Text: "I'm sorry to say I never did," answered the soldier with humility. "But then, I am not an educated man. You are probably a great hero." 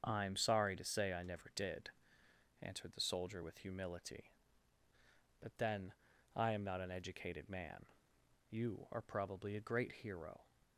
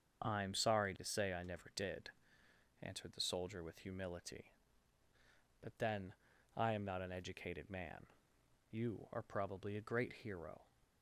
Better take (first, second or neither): neither